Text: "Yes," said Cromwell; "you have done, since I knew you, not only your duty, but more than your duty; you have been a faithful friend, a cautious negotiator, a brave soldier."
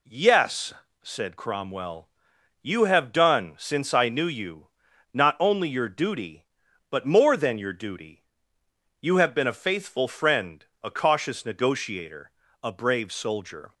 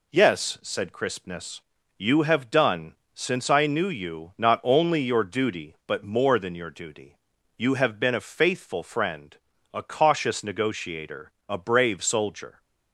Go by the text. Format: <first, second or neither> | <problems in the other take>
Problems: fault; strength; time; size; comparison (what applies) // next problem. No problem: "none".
first | says "Crispness" for "Cromwell"; at 0.9 s